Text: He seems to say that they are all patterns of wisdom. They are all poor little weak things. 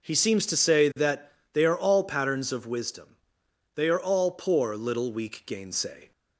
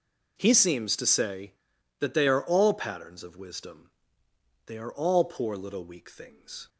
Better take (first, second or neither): second